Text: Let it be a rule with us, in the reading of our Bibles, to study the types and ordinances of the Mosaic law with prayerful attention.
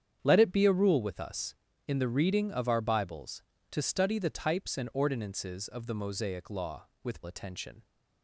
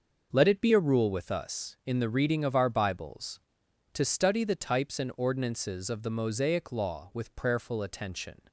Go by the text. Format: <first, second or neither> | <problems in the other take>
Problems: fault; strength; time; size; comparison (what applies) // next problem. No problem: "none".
second | starts louder than the rest; strong; until 1.2 s; 8.5 dB; noticeable in the second // skips "prayerful"; at 7.2 s